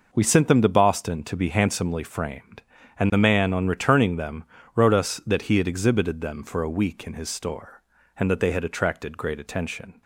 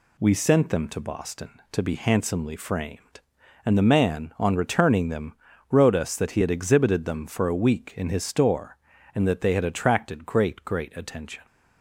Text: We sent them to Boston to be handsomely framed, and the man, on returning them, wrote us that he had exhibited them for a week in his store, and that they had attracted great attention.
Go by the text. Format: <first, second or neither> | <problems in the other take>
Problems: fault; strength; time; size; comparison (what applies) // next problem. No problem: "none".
first | says "great" twice; at 10.6 s